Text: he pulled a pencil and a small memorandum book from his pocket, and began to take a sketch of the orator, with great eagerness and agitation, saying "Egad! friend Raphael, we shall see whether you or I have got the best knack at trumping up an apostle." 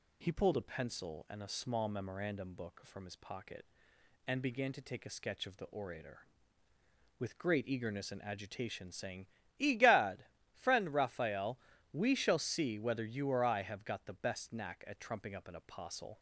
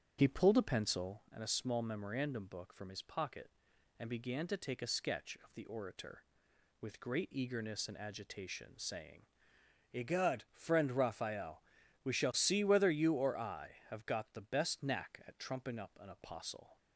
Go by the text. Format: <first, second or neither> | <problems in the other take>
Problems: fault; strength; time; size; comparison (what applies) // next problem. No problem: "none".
first | starts louder than the rest; strong; until 1.2 s; 8 dB // pauses between "saying" and "Egad"; noticeable; at 9.2 s; 0.72 s long; slight in the first